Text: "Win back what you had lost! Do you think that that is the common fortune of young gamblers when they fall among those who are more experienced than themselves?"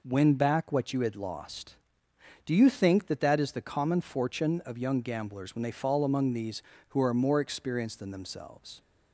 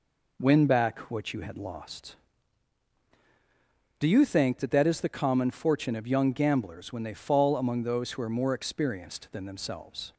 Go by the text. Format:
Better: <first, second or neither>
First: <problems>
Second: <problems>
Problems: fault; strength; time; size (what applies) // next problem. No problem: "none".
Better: second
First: says "these" for "those"; at 6.3 s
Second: none